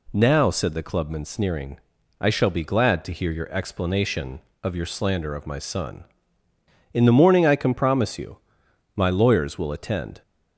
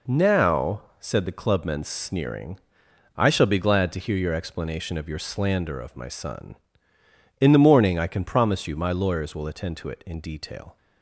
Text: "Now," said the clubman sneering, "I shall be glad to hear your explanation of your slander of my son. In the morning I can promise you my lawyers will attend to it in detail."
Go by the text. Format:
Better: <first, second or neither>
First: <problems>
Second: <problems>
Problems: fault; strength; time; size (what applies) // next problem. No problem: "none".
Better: second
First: pauses between "you" and "my"; noticeable; at 8.3 s; 0.58 s long // stops before "to it in detail"; at 10.2 s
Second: none